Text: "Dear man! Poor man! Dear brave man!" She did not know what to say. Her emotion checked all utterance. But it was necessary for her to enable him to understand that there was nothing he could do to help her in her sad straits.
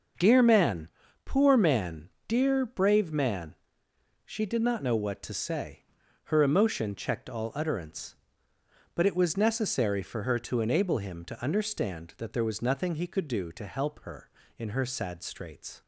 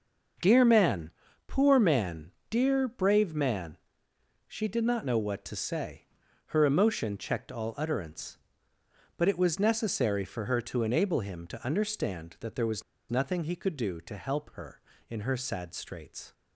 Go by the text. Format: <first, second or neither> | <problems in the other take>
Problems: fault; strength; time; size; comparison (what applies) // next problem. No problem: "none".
first | starts louder than the rest; until 1.7 s; 6.5 dB; also in the first // pauses between "was" and "nothing"; slight; at 12.8 s; 0.28 s long